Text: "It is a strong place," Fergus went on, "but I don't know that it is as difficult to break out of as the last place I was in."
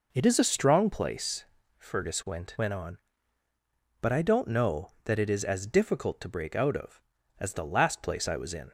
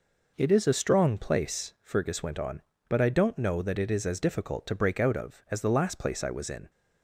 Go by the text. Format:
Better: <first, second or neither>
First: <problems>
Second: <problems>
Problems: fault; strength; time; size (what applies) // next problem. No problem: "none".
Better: second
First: says "went" twice; at 2.5 s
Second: none